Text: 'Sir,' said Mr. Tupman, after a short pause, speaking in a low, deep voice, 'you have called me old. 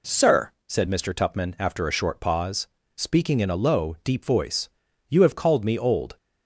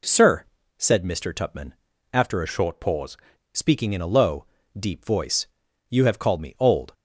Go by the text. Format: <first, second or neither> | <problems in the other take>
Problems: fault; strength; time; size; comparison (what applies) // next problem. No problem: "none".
first | changes voice from "short" to "pause"; from 2.4 to 3.1 s; 0.7 s long